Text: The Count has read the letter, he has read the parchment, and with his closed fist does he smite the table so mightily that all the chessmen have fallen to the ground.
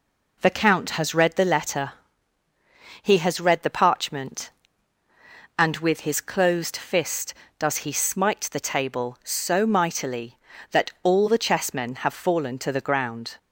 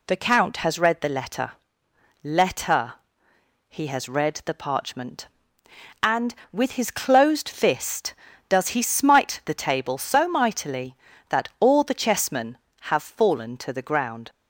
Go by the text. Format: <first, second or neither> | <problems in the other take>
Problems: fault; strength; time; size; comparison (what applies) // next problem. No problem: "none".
first | says "letter" twice; at 2.2 s